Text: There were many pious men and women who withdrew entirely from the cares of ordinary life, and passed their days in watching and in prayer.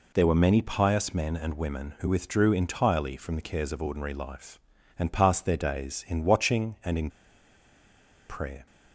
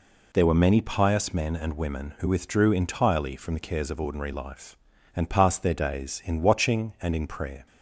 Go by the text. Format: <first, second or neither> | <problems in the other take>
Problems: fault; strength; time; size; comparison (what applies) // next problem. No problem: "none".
second | pauses between "in" and "prayer"; at 7.0 s; 1.2 s long